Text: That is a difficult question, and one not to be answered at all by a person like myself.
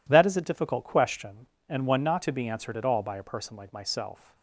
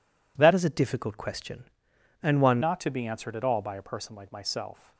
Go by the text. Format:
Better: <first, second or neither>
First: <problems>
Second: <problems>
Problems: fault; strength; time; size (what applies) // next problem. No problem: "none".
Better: first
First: none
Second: changes voice from "is" to "one"; from 0.5 to 2.5 s; 2.0 s long